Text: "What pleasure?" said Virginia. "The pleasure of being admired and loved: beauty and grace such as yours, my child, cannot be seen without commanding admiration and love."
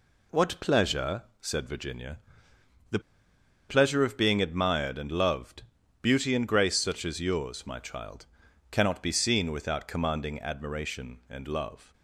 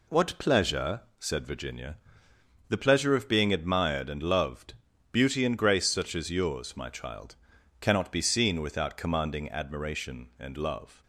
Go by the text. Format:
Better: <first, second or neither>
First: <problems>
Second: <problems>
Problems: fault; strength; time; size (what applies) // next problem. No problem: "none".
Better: second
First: pauses between "The" and "pleasure"; noticeable; at 2.9 s; 0.69 s long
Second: none